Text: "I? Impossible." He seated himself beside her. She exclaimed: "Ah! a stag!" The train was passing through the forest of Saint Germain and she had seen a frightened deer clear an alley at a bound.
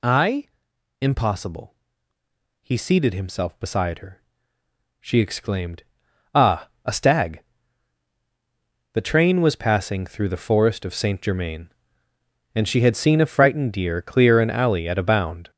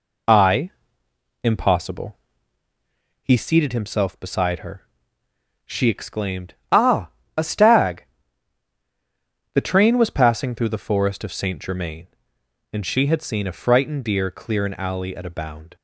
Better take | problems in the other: second | gets louder; throughout; 7 dB

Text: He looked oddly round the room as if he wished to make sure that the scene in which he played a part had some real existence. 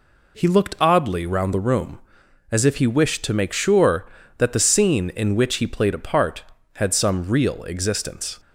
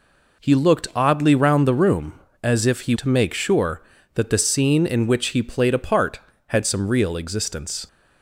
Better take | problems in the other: first | skips "wished"; at 2.9 s

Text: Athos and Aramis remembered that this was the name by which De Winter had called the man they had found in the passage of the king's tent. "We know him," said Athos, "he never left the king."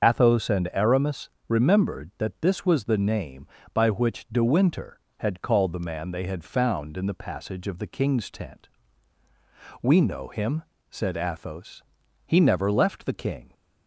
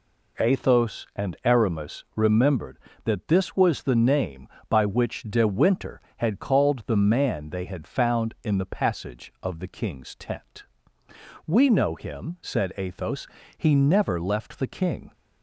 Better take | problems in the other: second | loses the start of "Athos"; at 0.0 s; 65 ms // starts louder than the rest; until 1.0 s; 6.5 dB // pauses between "Aramis" and "remembered"; slight; at 1.2 s; 0.18 s long

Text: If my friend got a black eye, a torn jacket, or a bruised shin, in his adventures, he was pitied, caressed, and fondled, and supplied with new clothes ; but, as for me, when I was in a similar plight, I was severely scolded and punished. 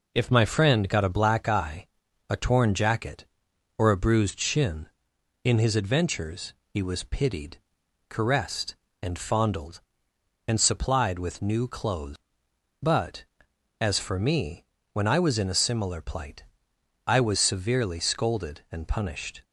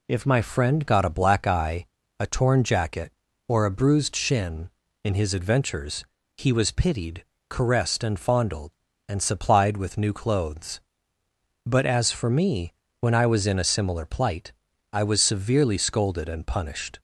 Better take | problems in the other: neither | none

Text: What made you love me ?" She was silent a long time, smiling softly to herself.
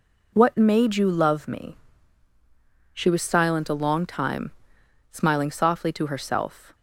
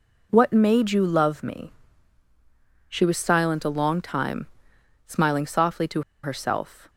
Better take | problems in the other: first | pauses between "to" and "herself"; slight; at 6.0 s; 0.21 s long

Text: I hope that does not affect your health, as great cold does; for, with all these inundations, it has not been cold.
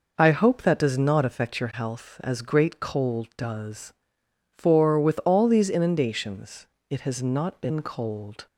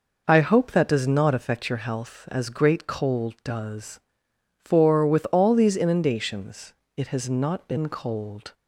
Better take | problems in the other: neither | none

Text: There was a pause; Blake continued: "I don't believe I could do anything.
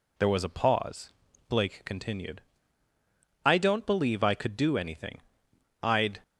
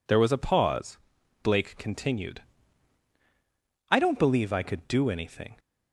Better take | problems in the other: second | goes on to say "I'd"; slight; from 5.8 s on; 0.38 s long

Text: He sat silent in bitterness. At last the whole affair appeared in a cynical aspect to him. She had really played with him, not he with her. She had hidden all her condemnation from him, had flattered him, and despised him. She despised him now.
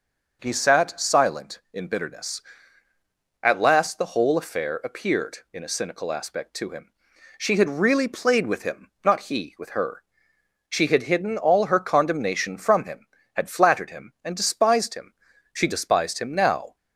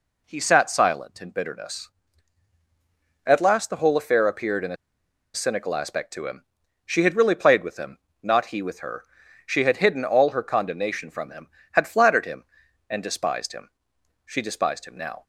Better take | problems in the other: first | pauses between "a" and "cynical"; noticeable; at 4.7 s; 0.59 s long

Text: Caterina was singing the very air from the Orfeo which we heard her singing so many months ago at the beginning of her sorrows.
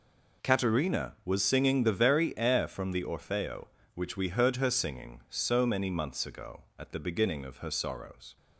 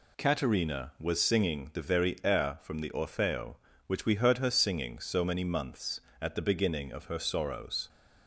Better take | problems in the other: first | skips "ago"; at 6.1 s

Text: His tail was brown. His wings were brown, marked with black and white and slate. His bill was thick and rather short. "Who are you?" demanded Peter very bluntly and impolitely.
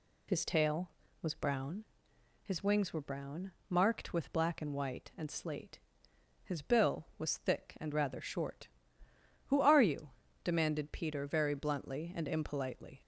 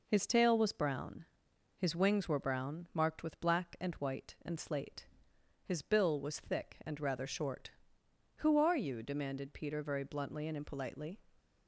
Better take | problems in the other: neither | none

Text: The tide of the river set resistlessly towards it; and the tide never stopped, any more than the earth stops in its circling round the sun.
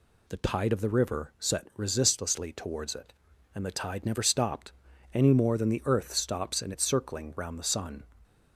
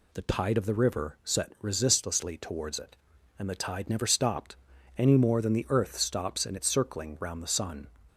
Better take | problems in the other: neither | none

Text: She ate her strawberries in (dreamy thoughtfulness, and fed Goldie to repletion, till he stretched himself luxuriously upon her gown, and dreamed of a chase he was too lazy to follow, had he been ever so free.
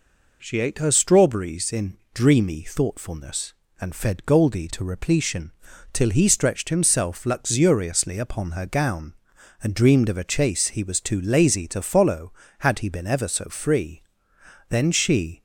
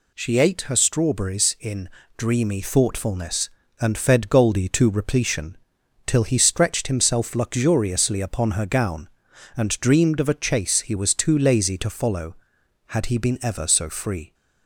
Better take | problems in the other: second | goes on to say "Then she"; noticeable; from 14.7 s on; 0.72 s long

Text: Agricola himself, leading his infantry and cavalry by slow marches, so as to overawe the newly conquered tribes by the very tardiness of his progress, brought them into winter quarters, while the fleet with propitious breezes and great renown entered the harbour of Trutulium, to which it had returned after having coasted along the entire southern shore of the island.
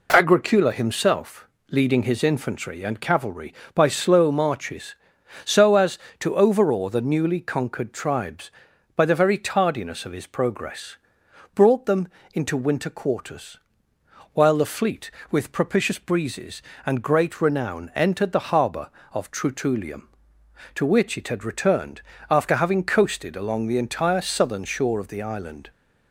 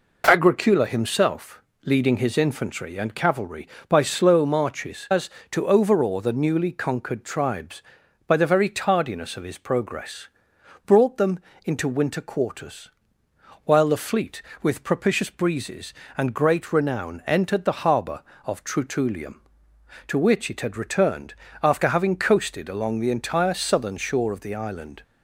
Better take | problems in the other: first | skips "so"; at 5.0 s // pauses between "them" and "into"; slight; at 11.4 s; 0.24 s long; slight in the first // pauses between "returned" and "after"; slight; at 21.3 s; 0.30 s long; slight in the first

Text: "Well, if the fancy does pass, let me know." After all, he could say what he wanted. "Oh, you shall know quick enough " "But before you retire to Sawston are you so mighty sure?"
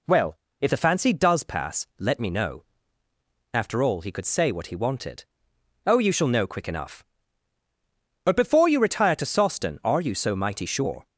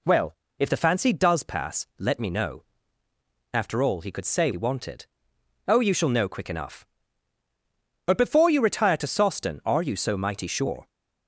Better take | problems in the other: first | skips "what"; at 4.5 s

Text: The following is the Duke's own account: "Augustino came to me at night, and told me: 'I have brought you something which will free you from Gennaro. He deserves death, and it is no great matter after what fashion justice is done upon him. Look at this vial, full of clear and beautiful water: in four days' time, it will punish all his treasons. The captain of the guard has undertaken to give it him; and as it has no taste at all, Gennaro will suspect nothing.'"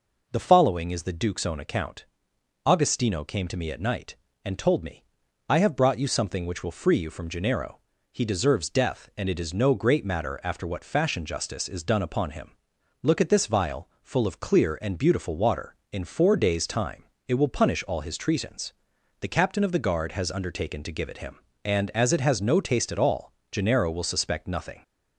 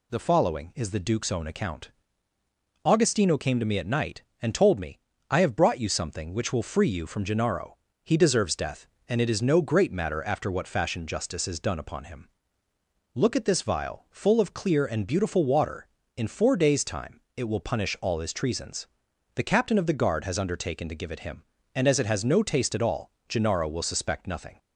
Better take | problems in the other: neither | none

